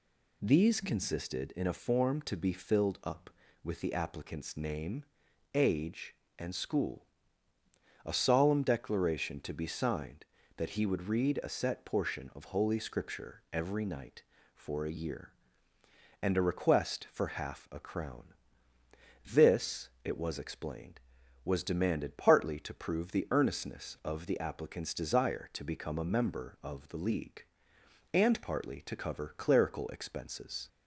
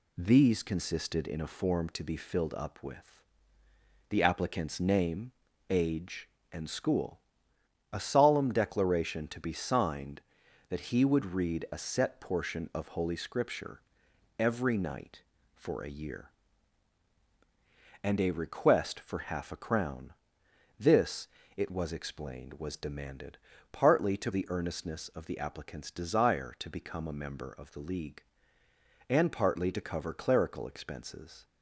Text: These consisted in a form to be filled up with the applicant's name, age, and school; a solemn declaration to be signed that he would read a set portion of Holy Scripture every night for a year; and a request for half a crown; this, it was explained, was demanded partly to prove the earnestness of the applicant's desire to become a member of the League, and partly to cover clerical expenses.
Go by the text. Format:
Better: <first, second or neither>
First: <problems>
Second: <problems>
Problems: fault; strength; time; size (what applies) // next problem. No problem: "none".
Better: first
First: none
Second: pauses between "with" and "the"; noticeable; at 3.1 s; 0.90 s long // pauses between "Scripture" and "every"; noticeable; at 13.8 s; 0.58 s long // pauses between "demanded" and "partly"; slight; at 23.3 s; 0.36 s long // skips "prove"; at 24.3 s